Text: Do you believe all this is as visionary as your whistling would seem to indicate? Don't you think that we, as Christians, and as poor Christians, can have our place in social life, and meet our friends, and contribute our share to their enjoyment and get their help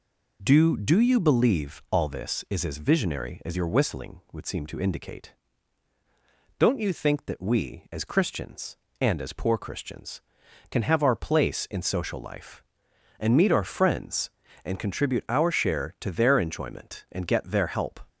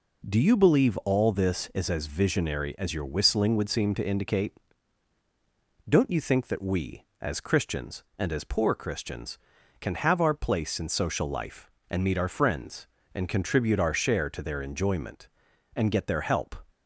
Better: second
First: says "Do" twice; at 0.7 s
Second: none

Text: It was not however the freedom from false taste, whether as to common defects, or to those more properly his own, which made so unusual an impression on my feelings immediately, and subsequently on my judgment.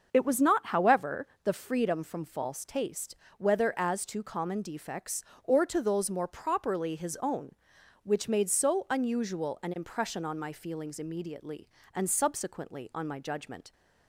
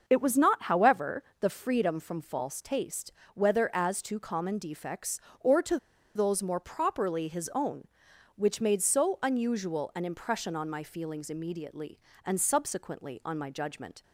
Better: first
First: starts louder than the rest; until 1.1 s; 6.5 dB // pauses between "however" and "the"; slight; at 1.2 s; 0.18 s long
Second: starts louder than the rest; until 1.0 s; 6.5 dB // pauses between "however" and "the"; slight; at 1.2 s; 0.18 s long // pauses between "to" and "those"; at 5.7 s; 0.38 s long

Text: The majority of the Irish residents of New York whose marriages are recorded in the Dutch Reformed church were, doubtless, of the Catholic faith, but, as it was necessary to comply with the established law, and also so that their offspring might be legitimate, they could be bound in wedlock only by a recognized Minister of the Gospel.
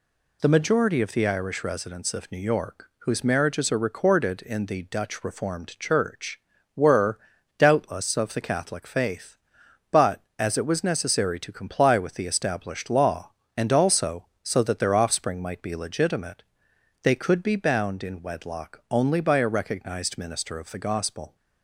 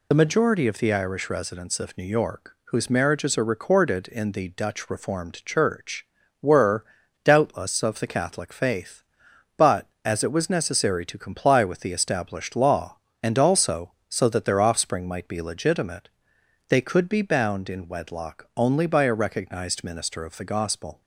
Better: first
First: none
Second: loses the start of "The"; at 0.1 s; 40 ms

